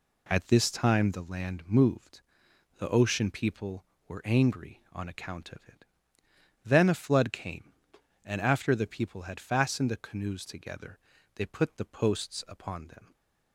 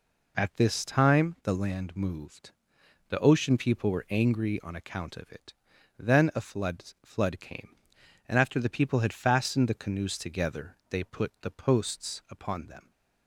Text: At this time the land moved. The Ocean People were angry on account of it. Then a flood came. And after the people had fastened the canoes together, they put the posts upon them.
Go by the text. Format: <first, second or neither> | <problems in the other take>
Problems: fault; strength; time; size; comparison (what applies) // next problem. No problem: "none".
first | says "flood" twice; at 7.0 s